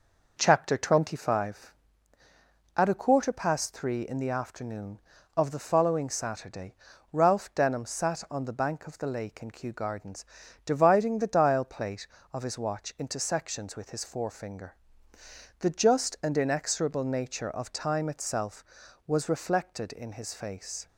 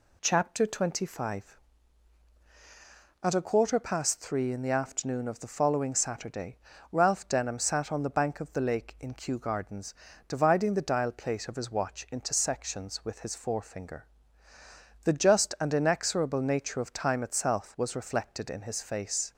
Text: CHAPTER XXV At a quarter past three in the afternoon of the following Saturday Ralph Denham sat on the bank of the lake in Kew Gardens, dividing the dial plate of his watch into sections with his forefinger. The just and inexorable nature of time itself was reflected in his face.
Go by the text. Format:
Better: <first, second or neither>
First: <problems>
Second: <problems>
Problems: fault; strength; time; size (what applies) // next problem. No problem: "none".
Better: second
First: starts louder than the rest; noticeable; until 2.0 s; 5.5 dB // pauses between "Saturday" and "Ralph"; slight; at 6.7 s; 0.36 s long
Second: pauses between "Saturday" and "Ralph"; slight; at 6.5 s; 0.34 s long